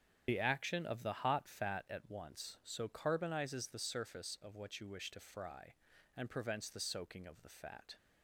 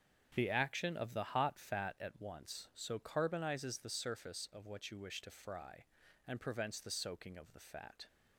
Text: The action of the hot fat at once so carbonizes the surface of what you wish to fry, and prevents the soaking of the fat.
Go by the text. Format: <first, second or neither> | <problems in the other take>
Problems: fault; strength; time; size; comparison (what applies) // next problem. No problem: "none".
second | loses the start of "The"; at 0.2 s; 70 ms // starts louder than the rest; strong; until 1.2 s; 8 dB; strong in the second